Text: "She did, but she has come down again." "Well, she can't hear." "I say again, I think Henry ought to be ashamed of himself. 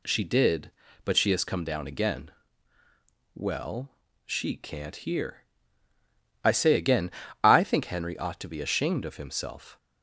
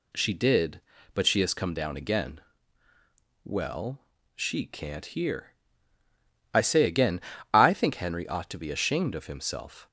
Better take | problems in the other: neither | none

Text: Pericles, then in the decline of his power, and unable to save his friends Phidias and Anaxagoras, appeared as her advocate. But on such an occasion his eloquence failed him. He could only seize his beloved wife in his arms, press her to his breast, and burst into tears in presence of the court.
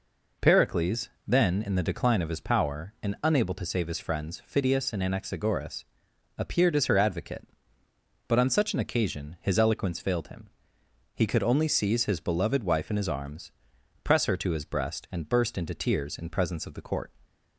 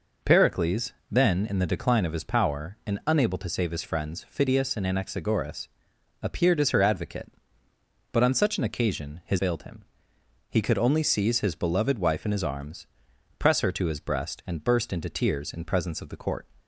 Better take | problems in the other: first | skips "eloquence"; at 9.3 s

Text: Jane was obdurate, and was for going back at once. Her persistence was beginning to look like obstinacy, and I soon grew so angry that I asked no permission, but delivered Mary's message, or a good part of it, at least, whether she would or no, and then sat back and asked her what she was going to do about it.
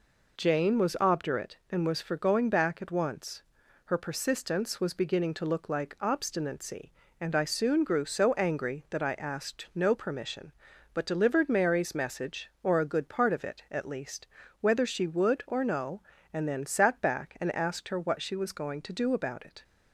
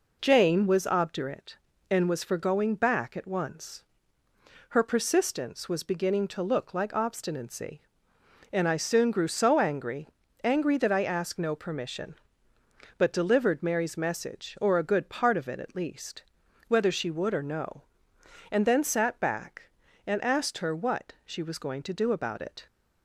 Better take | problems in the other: first | says "angry" twice; at 10.4 s

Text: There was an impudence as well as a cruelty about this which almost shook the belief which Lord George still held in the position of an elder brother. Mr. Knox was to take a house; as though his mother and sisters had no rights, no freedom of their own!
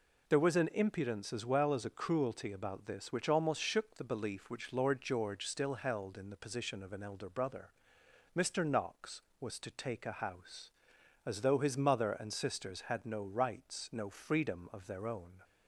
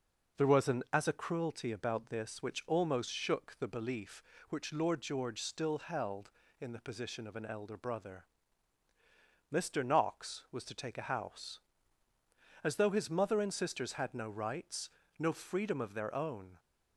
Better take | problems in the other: first | skips "impudence as well"; at 0.8 s

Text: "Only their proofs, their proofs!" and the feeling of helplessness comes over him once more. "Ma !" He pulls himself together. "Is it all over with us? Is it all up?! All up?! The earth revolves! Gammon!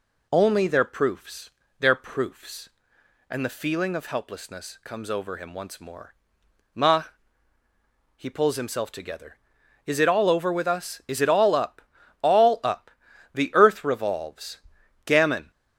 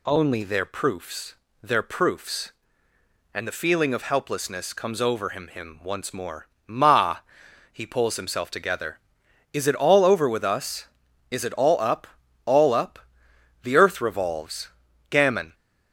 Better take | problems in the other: first | says "him" twice; at 5.4 s

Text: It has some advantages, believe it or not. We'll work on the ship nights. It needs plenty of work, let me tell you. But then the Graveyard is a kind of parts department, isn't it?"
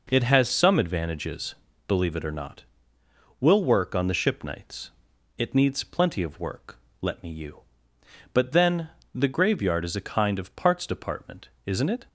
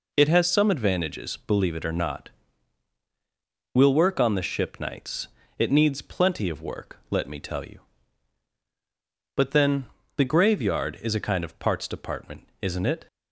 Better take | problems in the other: second | skips "tell"; at 7.2 s // pauses between "then" and "the"; slight; at 8.8 s; 0.26 s long; slight in the second

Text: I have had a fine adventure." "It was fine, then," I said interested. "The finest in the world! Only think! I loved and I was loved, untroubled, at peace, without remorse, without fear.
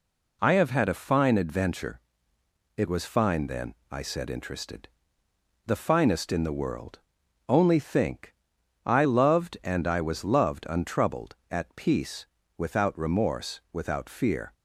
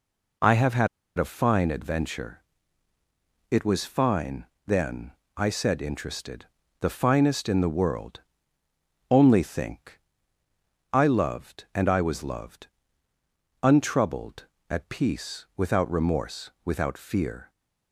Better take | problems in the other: first | pauses between "had" and "a"; slight; at 0.8 s; 0.31 s long

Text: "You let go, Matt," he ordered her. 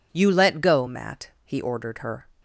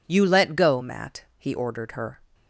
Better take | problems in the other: neither | none

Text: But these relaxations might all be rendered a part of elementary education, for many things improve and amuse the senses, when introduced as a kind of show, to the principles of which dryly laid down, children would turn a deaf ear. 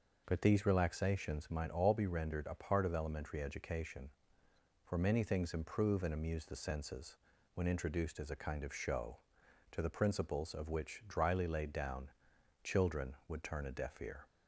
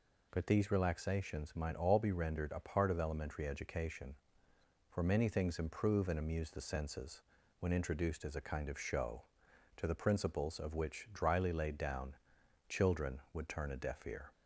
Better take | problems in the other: second | starts louder than the rest; noticeable; until 1.7 s; 6 dB

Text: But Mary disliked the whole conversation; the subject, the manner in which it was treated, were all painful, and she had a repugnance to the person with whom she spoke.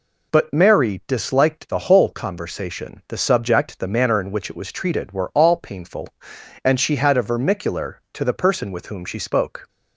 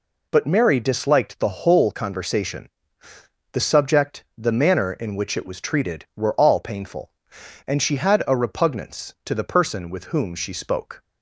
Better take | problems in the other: second | says "vermicular" for "repugnance"; at 7.2 s

